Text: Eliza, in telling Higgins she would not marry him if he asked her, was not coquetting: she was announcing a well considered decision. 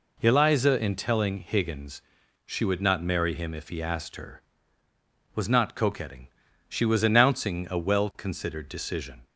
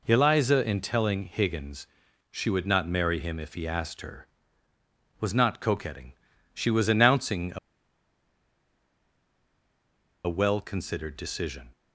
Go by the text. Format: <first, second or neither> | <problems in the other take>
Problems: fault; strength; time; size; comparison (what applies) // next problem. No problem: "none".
first | pauses between "Higgins" and "she"; noticeable; at 1.8 s; 0.46 s long; noticeable in the first // pauses between "a" and "well"; strong; at 7.5 s; 2.6 s long